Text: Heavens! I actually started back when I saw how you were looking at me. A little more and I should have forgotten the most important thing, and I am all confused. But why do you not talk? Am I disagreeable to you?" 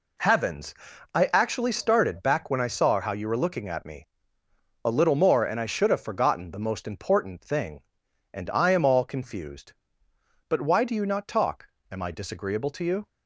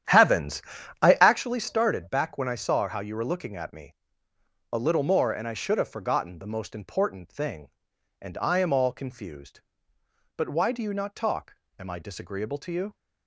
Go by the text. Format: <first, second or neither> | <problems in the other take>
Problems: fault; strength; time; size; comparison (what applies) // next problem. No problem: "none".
first | starts louder than the rest; strong; until 1.4 s; 10.5 dB